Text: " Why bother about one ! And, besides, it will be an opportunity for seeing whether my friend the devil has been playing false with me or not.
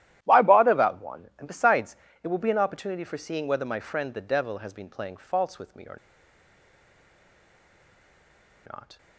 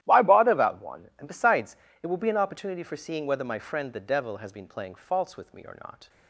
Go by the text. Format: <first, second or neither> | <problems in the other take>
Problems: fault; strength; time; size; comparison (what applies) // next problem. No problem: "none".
second | starts louder than the rest; strong; until 1.2 s; 13 dB; strong in the second // pauses between "or" and "not"; strong; at 5.9 s; 2.7 s long